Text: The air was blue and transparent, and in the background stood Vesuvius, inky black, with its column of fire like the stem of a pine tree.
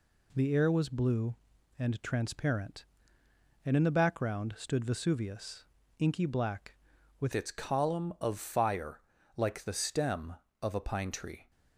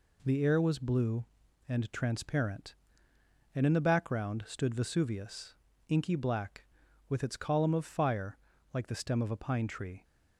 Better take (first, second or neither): second